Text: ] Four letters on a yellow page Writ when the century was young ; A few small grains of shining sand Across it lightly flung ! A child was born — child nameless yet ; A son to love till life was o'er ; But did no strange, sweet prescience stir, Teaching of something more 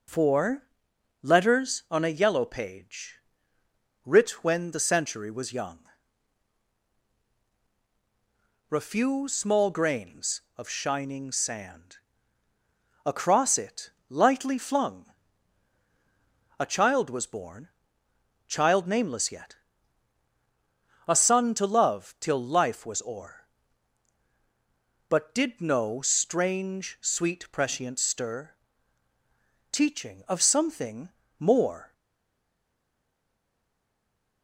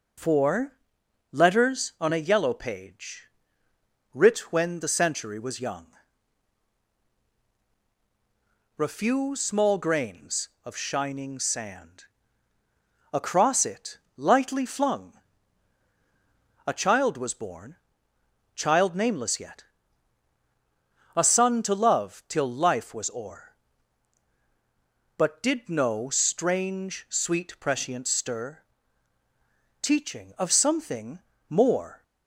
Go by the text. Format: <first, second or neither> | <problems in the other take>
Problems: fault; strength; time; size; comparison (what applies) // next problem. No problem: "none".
second | pauses between "Four" and "letters"; noticeable; at 0.6 s; 0.58 s long; noticeable in the second // pauses between "page" and "Writ"; noticeable; at 3.1 s; 0.88 s long; noticeable in the second // pauses between "sand" and "Across"; at 11.9 s; 1.0 s long; also in the second // pauses between "it" and "lightly"; slight; at 13.9 s; 0.18 s long; slight in the second // pauses between "something" and "more"; slight; at 31.1 s; 0.28 s long; slight in the second // stays silent after the last word; strong; from 31.9 s on; 2.5 s long